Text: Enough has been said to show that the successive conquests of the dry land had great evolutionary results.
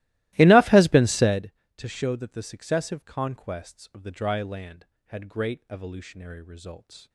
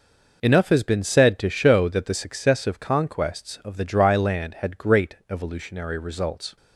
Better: second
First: starts louder than the rest; strong; until 1.5 s; 17.5 dB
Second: none

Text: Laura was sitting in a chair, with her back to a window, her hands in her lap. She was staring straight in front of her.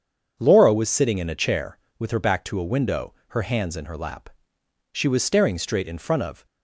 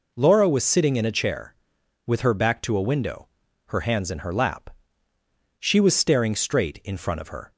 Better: second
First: starts louder than the rest; until 1.4 s; 7 dB // stops before "her"; at 6.4 s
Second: none

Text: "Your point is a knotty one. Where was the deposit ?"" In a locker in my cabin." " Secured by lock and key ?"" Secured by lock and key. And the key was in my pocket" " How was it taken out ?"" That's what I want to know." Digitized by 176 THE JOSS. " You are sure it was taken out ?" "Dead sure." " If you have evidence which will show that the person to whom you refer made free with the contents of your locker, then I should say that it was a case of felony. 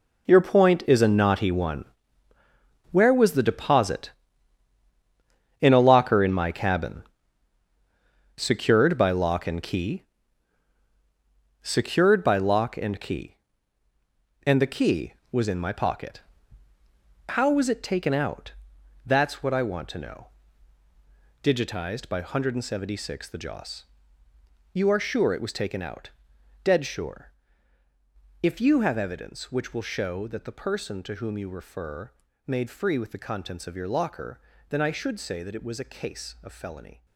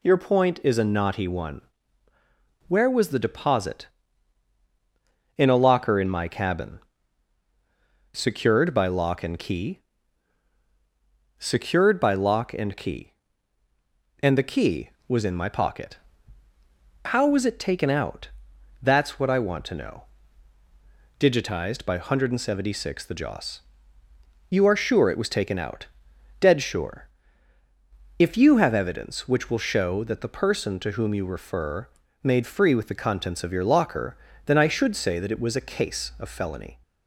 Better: second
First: gets quieter; throughout; 3.5 dB // pauses between "refer" and "made"; slight; at 32.1 s; 0.34 s long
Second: pauses between "refer" and "made"; slight; at 31.8 s; 0.34 s long

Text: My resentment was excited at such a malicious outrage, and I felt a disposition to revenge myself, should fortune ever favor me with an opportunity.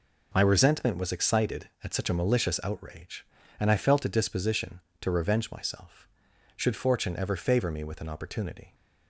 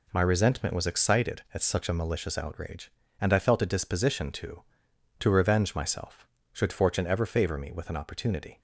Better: first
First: none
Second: says "to" twice; at 5.1 s

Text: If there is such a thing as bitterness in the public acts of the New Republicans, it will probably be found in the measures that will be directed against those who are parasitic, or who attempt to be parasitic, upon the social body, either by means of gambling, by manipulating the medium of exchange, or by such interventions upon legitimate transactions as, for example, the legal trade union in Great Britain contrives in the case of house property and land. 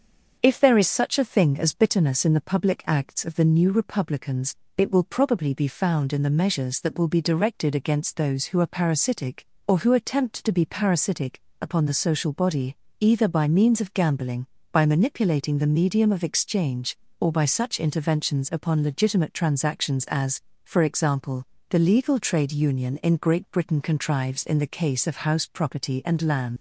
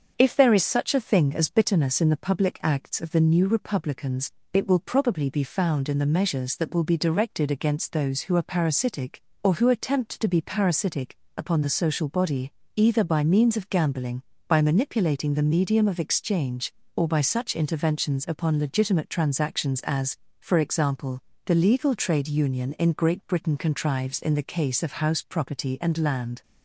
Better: second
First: starts louder than the rest; until 1.4 s; 6.5 dB // leaves "land" unfinished; at 26.5 s; 100 ms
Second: starts louder than the rest; until 1.1 s; 6.5 dB

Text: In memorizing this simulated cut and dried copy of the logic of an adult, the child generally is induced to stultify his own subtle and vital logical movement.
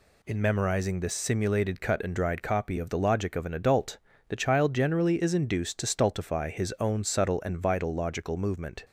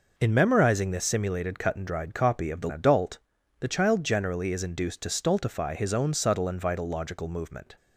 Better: first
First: none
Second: skips "logic of an"; at 2.7 s

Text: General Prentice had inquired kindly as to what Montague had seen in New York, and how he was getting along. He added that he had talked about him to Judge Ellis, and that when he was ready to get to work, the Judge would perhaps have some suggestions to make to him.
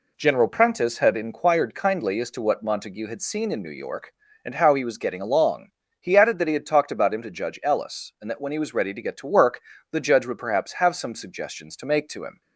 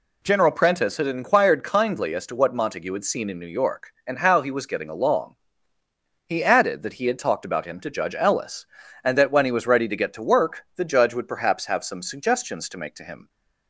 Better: neither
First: none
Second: none

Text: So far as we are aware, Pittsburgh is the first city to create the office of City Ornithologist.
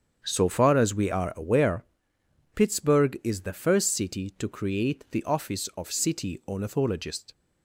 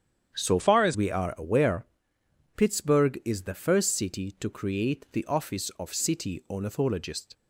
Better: first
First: starts louder than the rest; strong; until 1.2 s; 7.5 dB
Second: starts louder than the rest; strong; until 1.3 s; 8.5 dB // changes voice from "far" to "as"; from 0.5 to 0.9 s; 0.4 s long

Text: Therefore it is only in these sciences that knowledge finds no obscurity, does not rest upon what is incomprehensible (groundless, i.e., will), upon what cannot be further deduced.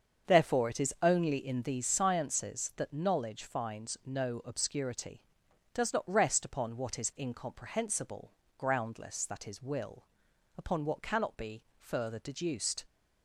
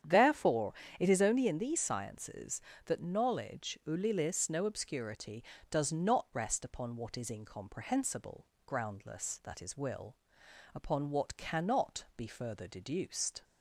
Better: first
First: starts louder than the rest; until 1.3 s; 7 dB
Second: starts louder than the rest; strong; until 1.3 s; 9 dB // pauses between "Therefore" and "it"; slight; at 0.7 s; 0.26 s long // says "ulilis" for "finds"; at 3.8 s

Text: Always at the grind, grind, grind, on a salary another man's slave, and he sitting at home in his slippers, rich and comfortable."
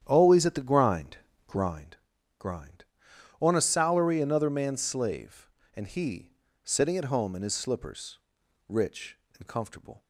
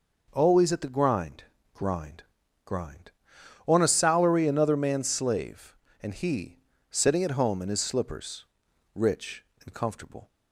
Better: second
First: starts louder than the rest; strong; until 1.8 s; 9.5 dB // pauses between "he" and "sitting"; slight; at 6.3 s; 0.32 s long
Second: pauses between "he" and "sitting"; slight; at 6.5 s; 0.32 s long

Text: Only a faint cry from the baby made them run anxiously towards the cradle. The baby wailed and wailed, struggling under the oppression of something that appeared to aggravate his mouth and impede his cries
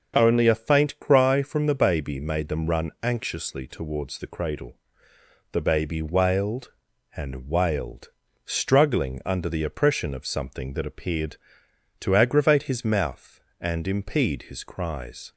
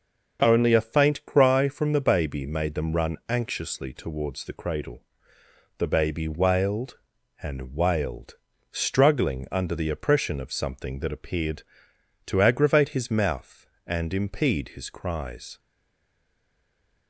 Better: first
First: starts louder than the rest; until 1.1 s; 6.5 dB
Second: starts louder than the rest; until 1.4 s; 6.5 dB // stays silent after the last word; noticeable; from 15.5 s on; 1.5 s long

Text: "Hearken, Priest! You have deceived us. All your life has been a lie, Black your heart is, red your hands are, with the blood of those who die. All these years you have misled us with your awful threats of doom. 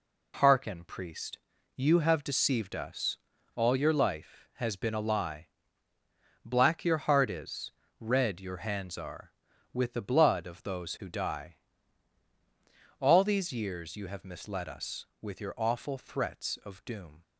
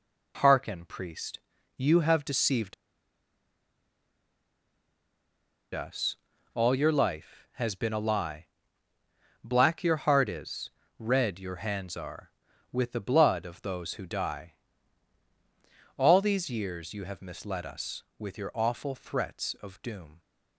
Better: first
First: none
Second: pauses between "deceived" and "us"; strong; at 2.7 s; 2.9 s long

